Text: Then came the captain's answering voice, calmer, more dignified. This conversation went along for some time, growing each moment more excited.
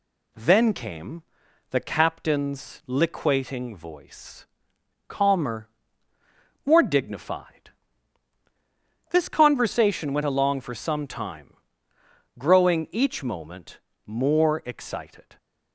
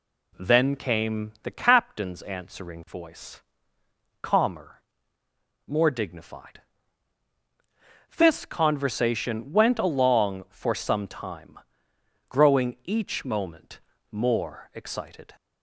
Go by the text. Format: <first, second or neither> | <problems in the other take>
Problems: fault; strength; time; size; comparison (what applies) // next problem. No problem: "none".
second | pauses between "came" and "the"; noticeable; at 1.2 s; 0.48 s long // says "liquating" for "answering"; at 2.8 s // pauses between "moment" and "more"; slight; at 13.7 s; 0.26 s long; slight in the second